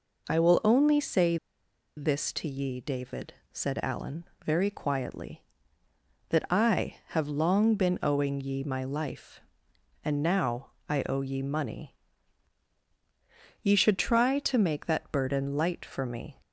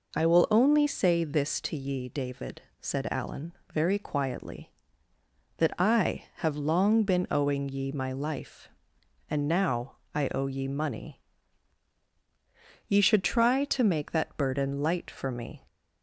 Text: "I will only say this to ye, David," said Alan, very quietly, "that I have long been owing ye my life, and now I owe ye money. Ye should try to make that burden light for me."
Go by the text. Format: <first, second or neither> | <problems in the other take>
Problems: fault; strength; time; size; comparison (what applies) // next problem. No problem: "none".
second | pauses between "say" and "this"; noticeable; at 1.3 s; 0.61 s long // pauses between "now" and "I"; slight; at 10.7 s; 0.18 s long; slight in the second